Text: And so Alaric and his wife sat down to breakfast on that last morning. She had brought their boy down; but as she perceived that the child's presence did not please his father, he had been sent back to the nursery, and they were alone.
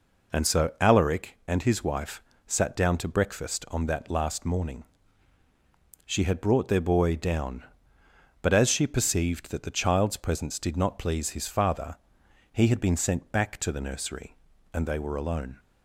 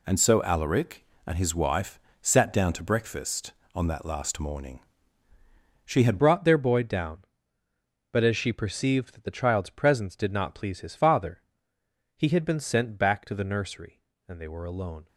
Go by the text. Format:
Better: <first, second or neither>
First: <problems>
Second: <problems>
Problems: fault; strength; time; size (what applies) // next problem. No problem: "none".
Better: first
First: pauses between "wife" and "sat"; slight; at 2.2 s; 0.24 s long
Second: pauses between "wife" and "sat"; slight; at 1.9 s; 0.22 s long // changes voice at "brought"; from 6.1 s on; 8.9 s long